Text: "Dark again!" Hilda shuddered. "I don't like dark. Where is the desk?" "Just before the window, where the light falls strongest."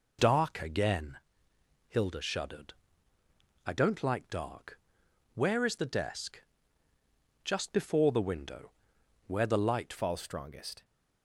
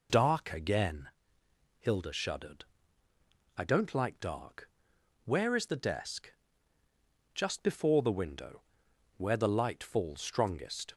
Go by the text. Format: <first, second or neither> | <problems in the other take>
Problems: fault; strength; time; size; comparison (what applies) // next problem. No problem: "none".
second | changes voice at "falls"; from 9.9 s on; 0.9 s long